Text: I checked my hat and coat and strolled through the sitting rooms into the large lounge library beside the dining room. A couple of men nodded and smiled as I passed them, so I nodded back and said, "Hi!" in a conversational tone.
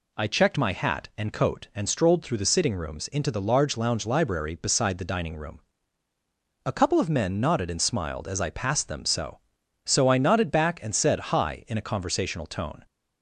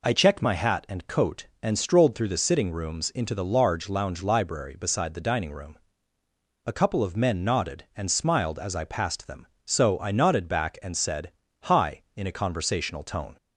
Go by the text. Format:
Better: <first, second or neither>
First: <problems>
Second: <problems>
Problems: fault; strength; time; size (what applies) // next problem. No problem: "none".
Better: second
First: says "so" twice; at 9.8 s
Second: none